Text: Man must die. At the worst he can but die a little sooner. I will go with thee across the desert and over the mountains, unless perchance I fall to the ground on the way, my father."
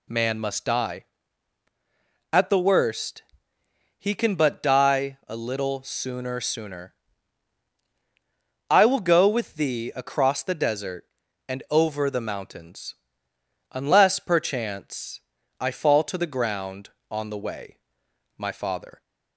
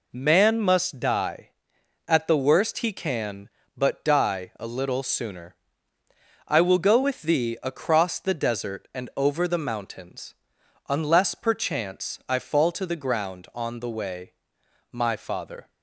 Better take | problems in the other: second | pauses between "worst" and "he"; noticeable; at 3.2 s; 0.78 s long // says "sooner" twice; at 6.4 s // pauses between "perchance" and "I"; at 15.2 s; 0.38 s long

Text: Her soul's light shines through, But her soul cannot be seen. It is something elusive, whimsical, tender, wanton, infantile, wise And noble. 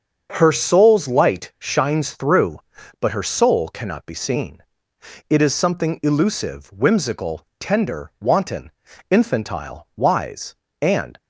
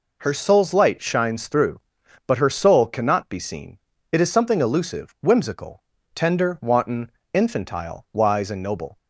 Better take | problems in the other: second | starts louder than the rest; until 1.3 s; 6.5 dB // stops before "noble"; at 11.1 s

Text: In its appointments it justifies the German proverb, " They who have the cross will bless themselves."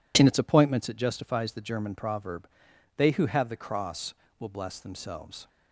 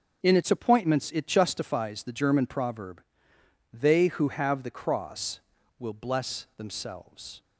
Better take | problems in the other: neither | none

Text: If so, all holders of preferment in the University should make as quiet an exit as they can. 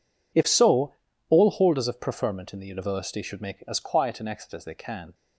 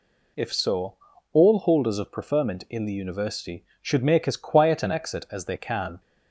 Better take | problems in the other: neither | none

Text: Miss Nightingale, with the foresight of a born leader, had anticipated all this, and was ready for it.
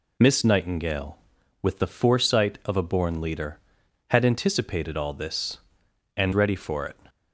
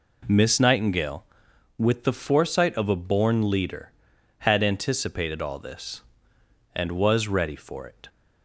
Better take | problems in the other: second | skips "was"; at 6.3 s

